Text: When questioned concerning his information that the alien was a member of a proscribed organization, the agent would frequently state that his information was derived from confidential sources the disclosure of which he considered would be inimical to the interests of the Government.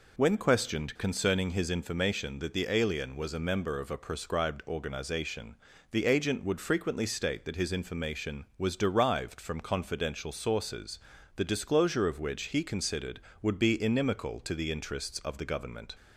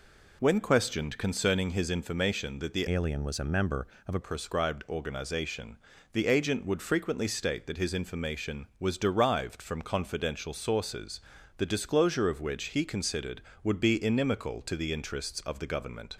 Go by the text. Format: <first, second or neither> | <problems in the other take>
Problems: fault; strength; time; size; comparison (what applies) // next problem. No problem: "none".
first | changes voice from "alien" to "a"; from 2.9 to 4.1 s; 1.2 s long // pauses between "sources" and "the"; at 11.2 s; 0.38 s long; also in the first